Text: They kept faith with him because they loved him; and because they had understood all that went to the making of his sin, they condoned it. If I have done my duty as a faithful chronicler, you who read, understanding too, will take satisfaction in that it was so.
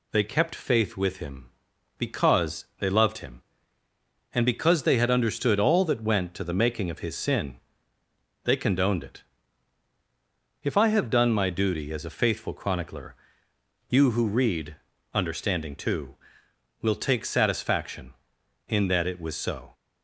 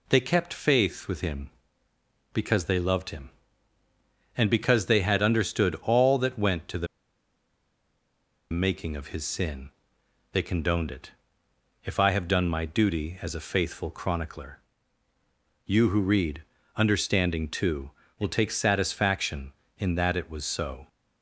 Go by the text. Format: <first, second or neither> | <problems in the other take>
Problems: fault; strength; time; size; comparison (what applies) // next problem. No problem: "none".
first | pauses between "the" and "making"; strong; at 6.8 s; 1.6 s long